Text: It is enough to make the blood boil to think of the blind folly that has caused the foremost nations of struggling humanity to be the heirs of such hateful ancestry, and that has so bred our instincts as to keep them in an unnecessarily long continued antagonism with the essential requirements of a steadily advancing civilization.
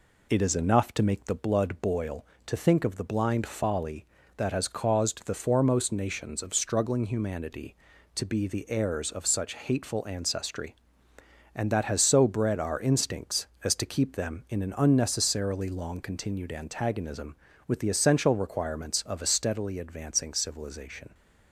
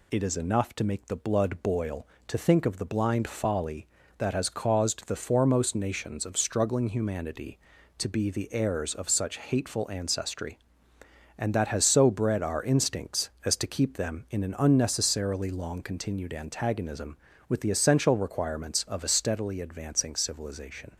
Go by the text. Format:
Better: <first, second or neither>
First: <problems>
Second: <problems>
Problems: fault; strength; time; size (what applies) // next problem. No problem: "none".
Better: second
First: starts louder than the rest; slight; until 1.6 s; 3 dB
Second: none